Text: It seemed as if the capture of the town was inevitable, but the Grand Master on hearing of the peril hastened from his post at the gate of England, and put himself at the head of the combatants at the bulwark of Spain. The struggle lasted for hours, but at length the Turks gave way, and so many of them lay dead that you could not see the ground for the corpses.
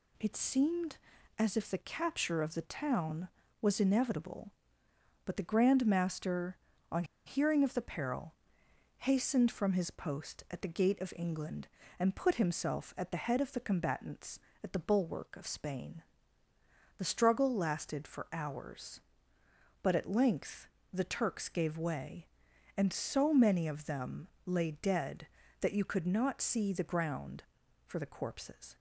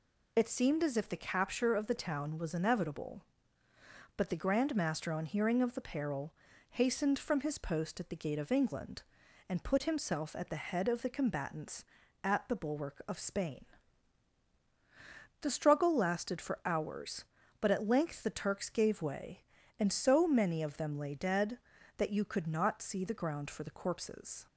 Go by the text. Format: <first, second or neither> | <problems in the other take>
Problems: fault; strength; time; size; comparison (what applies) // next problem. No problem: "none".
second | pauses between "on" and "hearing"; slight; at 7.0 s; 0.21 s long // pauses between "peril" and "hastened"; noticeable; at 8.3 s; 0.66 s long; also in the second // pauses between "length" and "the"; slight; at 20.6 s; 0.26 s long // pauses between "them" and "lay"; slight; at 24.2 s; 0.18 s long